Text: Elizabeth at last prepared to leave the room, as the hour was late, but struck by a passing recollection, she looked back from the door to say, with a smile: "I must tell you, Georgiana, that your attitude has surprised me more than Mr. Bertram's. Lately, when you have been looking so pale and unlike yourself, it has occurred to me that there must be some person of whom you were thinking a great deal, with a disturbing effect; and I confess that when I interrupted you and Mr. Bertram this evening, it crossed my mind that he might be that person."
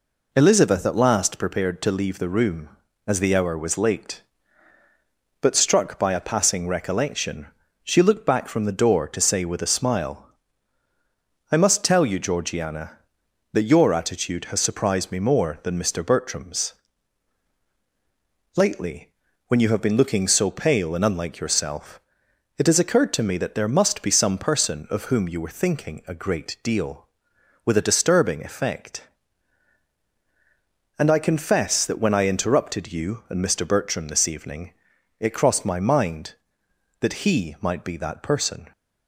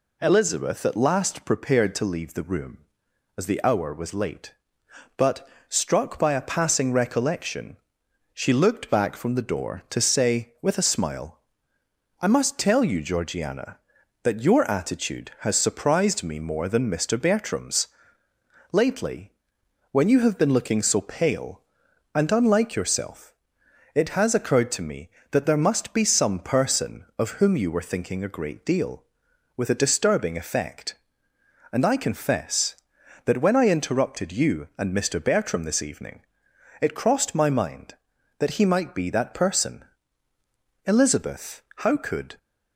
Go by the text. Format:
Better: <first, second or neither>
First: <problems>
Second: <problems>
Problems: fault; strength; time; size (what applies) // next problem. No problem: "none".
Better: first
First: none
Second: pauses between "but" and "struck"; slight; at 5.4 s; 0.22 s long // goes on to say "Elizabeth how could"; from 40.8 s on; 1.5 s long